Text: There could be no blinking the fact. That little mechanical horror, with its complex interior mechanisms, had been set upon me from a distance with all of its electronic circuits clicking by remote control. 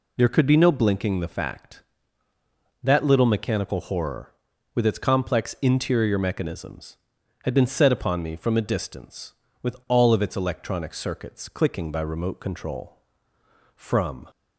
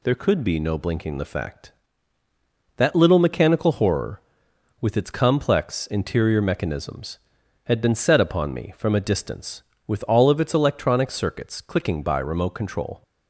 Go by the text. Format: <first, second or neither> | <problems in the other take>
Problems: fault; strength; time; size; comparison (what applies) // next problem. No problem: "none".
second | goes on to say "From"; from 13.7 s on; 0.52 s long